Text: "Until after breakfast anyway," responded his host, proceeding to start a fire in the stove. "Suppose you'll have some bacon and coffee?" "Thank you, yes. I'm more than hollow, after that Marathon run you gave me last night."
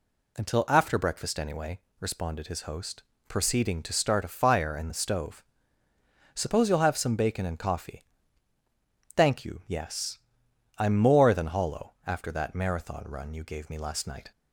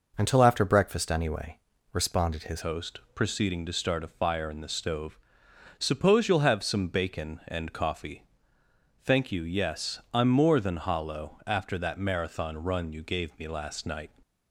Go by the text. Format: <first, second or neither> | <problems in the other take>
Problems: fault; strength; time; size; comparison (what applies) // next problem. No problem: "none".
first | changes voice at "host"; from 2.6 s on; 11.4 s long